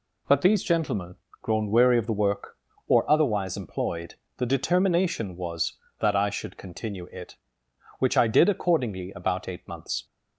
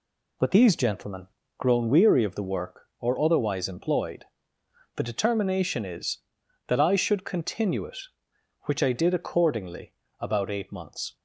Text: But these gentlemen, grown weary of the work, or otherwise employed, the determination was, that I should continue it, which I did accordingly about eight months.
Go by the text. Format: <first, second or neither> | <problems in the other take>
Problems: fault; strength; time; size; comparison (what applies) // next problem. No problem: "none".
first | says "is" for "was"; at 5.8 s // pauses between "accordingly" and "about"; slight; at 9.9 s; 0.26 s long